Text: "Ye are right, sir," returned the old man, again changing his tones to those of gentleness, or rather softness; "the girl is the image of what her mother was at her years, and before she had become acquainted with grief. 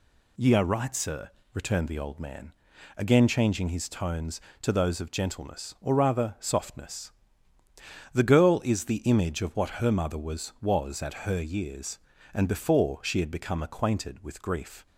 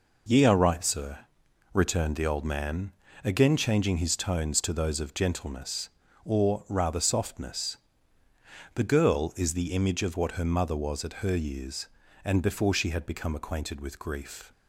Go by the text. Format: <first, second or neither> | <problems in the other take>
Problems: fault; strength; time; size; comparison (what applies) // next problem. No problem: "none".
second | says "was" twice; at 10.5 s